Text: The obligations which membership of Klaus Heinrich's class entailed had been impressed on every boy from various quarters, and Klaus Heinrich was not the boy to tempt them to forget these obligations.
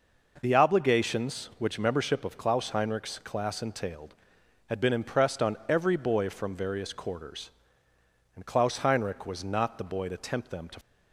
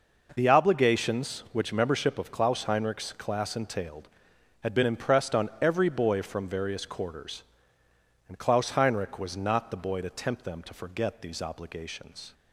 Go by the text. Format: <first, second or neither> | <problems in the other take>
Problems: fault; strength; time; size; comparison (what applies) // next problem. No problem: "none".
second | stops before "forget these obligations"; at 10.8 s